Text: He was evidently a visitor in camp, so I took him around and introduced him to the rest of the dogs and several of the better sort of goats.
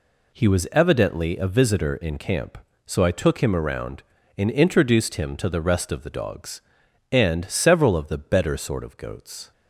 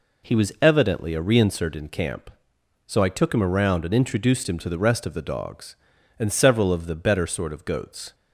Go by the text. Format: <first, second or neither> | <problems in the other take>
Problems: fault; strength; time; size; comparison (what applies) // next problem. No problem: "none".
first | says "reinsert" for "visitor"; at 1.2 s